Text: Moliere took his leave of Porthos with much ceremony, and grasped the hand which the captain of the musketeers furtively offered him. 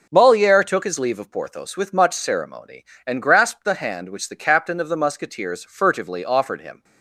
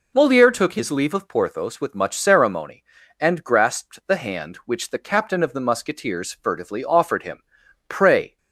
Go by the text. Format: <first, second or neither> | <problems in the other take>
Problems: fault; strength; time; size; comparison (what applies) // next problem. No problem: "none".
first | goes on to say "Pray"; slight; from 7.8 s on; 0.48 s long